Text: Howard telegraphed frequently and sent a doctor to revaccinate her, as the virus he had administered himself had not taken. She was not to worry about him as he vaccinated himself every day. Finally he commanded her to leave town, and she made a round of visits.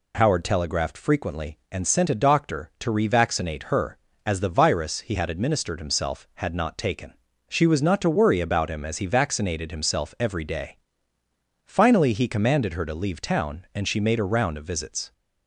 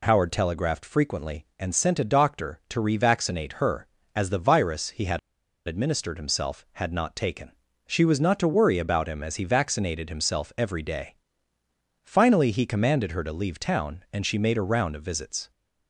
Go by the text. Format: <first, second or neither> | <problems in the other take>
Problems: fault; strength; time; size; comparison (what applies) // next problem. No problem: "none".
first | pauses between "had" and "administered"; noticeable; at 5.1 s; 0.48 s long